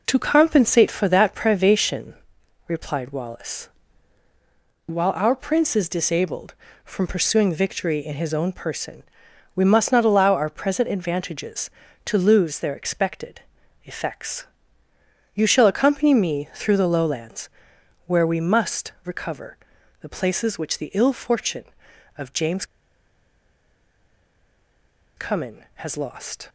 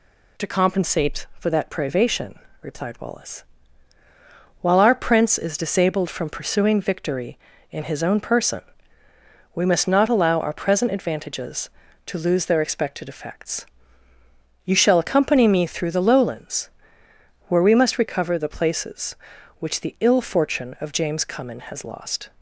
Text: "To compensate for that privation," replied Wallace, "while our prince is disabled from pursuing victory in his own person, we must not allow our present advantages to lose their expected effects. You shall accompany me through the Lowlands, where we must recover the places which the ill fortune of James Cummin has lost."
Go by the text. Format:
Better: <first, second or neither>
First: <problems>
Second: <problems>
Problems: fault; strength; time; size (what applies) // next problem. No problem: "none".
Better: second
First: pauses between "expected" and "effects"; at 13.4 s; 0.42 s long // pauses between "recover" and "the"; at 19.5 s; 0.44 s long // pauses between "James" and "Cummin"; strong; at 22.6 s; 2.5 s long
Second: none